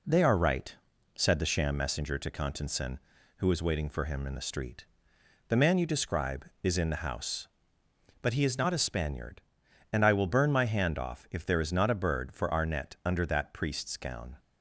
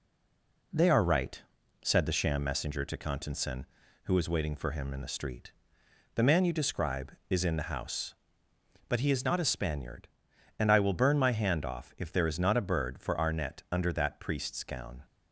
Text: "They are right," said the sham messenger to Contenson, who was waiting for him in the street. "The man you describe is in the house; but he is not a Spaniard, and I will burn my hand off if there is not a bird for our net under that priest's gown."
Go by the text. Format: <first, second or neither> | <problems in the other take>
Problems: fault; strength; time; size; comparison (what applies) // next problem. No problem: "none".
first | stays silent before the first word; slight; until 0.7 s; 0.7 s long